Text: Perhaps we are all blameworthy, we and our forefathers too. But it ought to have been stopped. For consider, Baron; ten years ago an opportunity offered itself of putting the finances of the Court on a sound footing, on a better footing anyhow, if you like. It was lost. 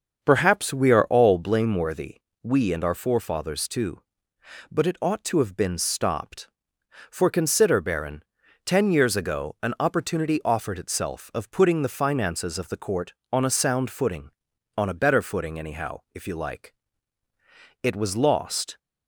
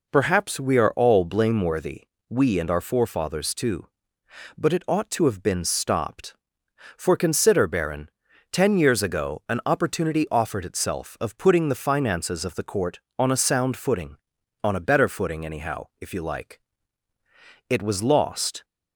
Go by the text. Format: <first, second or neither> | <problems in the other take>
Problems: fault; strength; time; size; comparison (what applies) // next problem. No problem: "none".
second | starts louder than the rest; until 1.4 s; 6.5 dB